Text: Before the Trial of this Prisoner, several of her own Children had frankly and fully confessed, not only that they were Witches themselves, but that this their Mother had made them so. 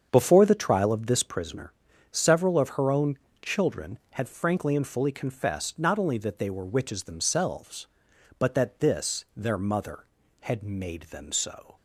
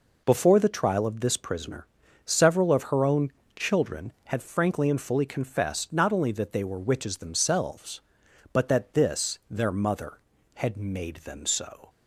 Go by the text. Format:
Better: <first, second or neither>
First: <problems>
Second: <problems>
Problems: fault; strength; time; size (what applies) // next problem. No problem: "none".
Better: second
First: starts louder than the rest; strong; until 1.5 s; 7.5 dB // pauses between "own" and "Children"; slight; at 3.1 s; 0.24 s long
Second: pauses between "own" and "Children"; slight; at 3.3 s; 0.24 s long